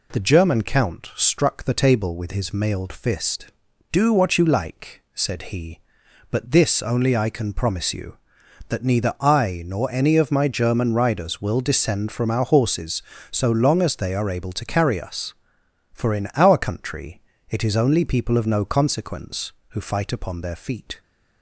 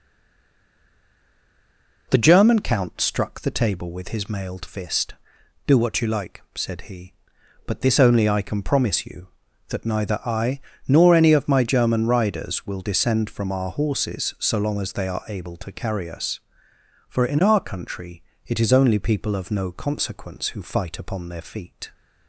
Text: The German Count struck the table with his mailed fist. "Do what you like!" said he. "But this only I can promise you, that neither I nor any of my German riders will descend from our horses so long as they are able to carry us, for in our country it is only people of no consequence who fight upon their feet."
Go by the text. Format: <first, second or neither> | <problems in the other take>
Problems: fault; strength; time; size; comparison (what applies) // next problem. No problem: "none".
first | stays silent before the first word; noticeable; until 2.0 s; 2.0 s long // pauses between "I" and "nor"; slight; at 10.5 s; 0.28 s long // pauses between "country" and "it"; slight; at 18.2 s; 0.24 s long; slight in the first